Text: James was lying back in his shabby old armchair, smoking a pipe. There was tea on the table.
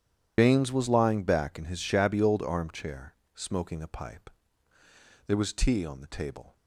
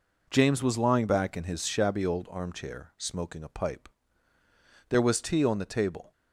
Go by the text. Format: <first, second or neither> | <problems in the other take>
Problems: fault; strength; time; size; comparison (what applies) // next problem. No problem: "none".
second | loses the start of "James"; at 0.3 s; 120 ms // starts louder than the rest; strong; until 1.3 s; 10.5 dB